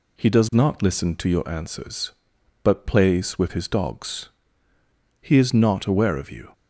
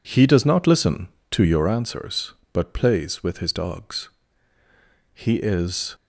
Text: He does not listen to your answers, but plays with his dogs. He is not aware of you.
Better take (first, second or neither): first